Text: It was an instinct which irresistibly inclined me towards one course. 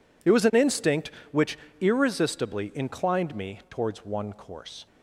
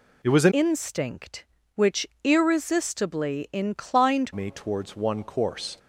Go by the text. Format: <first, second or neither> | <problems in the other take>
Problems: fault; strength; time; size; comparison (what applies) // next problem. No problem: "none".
first | changes voice from "instinct" to "inclined"; from 0.5 to 4.3 s; 3.8 s long // pauses between "which" and "irresistibly"; slight; at 2.0 s; 0.16 s long; slight in the first